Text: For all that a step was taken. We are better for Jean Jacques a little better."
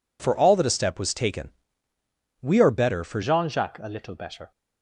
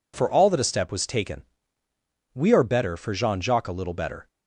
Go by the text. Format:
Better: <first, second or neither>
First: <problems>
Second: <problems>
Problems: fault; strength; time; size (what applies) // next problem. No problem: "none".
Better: second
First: changes voice at "Jean"; from 3.2 s on; 1.3 s long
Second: none